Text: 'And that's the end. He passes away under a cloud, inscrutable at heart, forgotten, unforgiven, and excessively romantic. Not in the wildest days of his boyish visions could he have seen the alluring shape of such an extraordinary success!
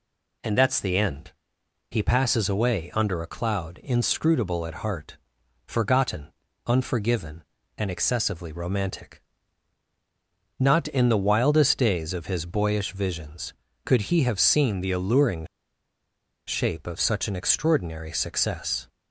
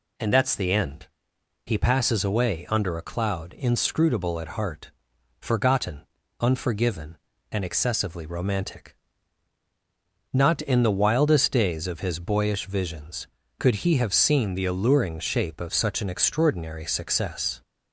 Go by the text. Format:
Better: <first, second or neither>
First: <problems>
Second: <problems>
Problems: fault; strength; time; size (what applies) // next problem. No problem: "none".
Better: second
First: pauses between "alluring" and "shape"; at 15.4 s; 1.0 s long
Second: none